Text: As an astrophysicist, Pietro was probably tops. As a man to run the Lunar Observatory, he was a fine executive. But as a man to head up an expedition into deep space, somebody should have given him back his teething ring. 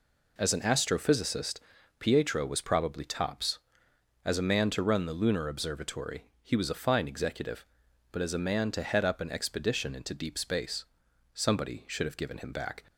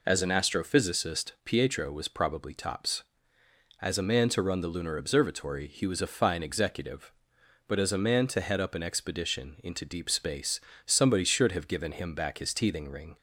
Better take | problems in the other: second | stops before "his teething ring"; at 12.8 s

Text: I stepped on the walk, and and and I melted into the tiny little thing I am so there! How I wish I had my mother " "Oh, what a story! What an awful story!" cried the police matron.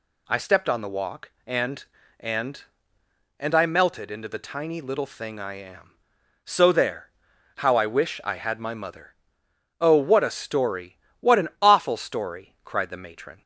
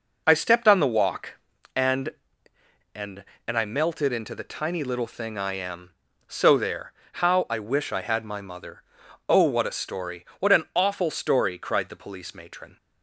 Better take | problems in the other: second | skips "police"; at 12.9 s

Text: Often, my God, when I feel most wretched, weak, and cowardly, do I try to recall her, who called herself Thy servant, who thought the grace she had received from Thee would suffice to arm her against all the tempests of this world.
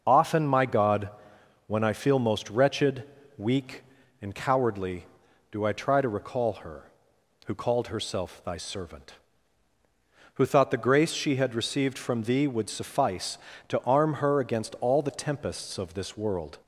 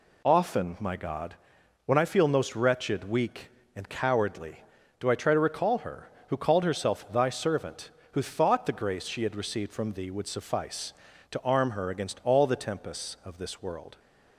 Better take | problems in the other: second | loses the start of "Often"; at 0.0 s; 35 ms

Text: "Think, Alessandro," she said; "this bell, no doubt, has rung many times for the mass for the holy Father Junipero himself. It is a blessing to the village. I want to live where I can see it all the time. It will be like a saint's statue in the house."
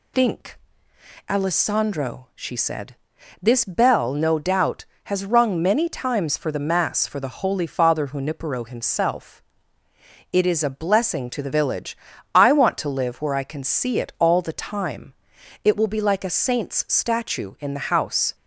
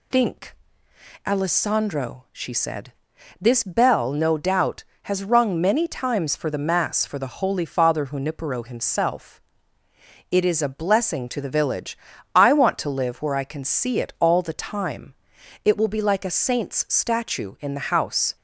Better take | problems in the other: neither | none

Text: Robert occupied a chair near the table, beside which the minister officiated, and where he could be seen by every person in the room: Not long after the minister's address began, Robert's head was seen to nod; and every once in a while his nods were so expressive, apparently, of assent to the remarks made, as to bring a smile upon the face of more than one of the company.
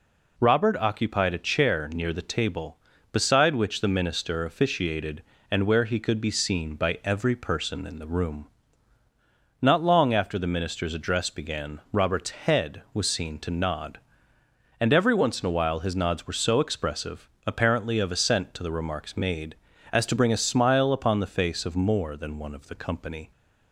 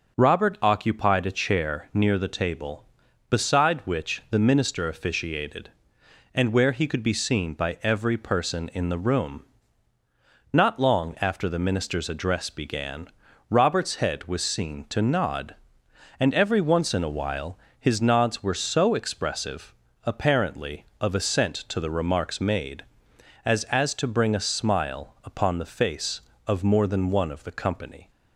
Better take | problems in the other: first | starts louder than the rest; until 1.2 s; 6.5 dB // pauses between "while" and "his"; slight; at 17.5 s; 0.22 s long // says "as" twice; at 23.6 s

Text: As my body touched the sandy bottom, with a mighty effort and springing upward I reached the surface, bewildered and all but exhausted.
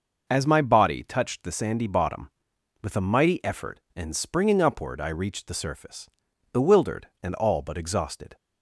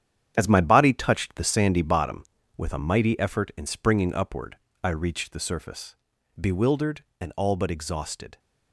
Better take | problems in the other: first | gets quieter; strong; throughout; 9.5 dB // pauses between "upward" and "I"; slight; at 4.5 s; 0.26 s long

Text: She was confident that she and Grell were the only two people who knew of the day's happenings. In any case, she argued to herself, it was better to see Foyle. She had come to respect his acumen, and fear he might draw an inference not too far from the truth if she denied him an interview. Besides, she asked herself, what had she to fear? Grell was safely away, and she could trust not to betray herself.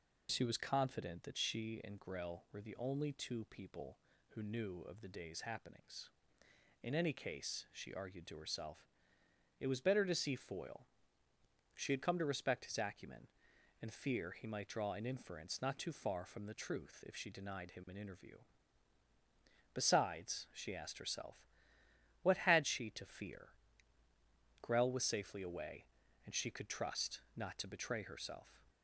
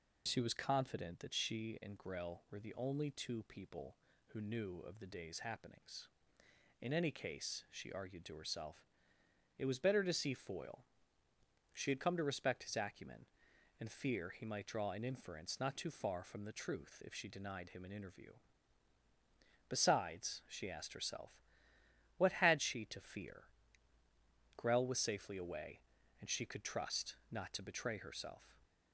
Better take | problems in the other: neither | pauses between "trust" and "not"; slight; the same in both

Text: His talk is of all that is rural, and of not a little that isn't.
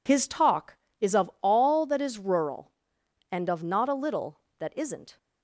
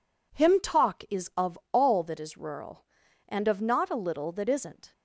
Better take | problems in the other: first | says "Him" for "His"; at 0.3 s

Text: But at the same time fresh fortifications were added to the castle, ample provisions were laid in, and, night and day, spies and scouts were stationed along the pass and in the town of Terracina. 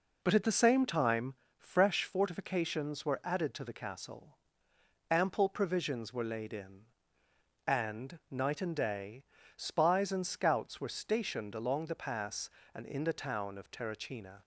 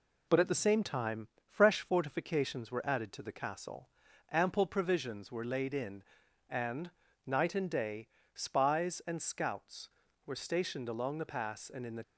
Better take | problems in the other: first | pauses between "time" and "fresh"; slight; at 1.2 s; 0.20 s long; slight in the first // stops before "town of Terracina"; at 12.0 s

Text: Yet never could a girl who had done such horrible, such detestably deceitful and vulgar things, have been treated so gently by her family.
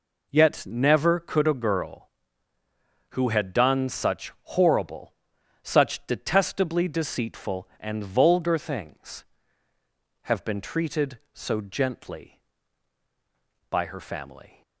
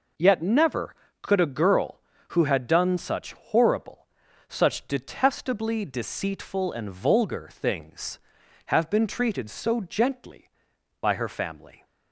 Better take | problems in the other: neither | none

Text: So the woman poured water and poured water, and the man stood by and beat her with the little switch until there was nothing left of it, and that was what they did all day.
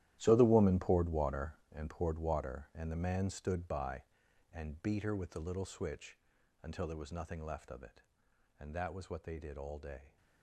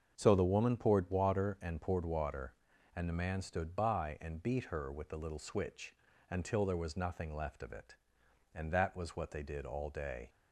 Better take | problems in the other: second | gets quieter; strong; throughout; 15 dB // starts louder than the rest; strong; until 1.2 s; 12.5 dB; also in the second // pauses between "switch" and "until"; at 6.1 s; 0.42 s long; slight in the second

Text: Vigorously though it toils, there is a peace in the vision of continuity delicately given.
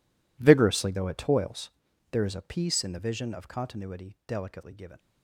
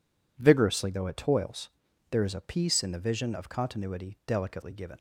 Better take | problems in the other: second | gets quieter; strong; throughout; 19 dB

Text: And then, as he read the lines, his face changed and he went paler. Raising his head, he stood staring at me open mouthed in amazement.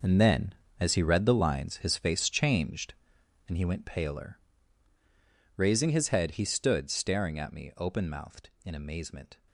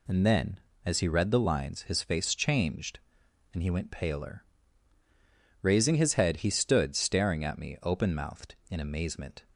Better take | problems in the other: second | gets quieter; strong; throughout; 11.5 dB

